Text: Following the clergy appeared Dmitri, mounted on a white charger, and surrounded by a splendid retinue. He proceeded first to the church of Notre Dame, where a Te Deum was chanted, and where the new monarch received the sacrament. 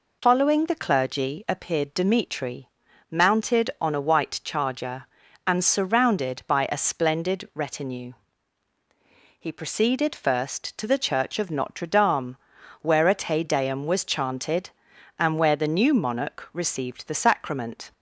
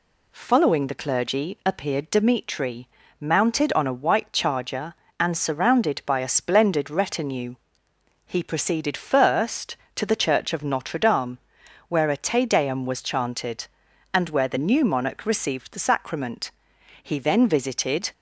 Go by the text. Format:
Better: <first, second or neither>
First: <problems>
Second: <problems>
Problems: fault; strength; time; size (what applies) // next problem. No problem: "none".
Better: first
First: none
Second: goes on to say "He then visited"; noticeable; from 17.0 s on; 1.1 s long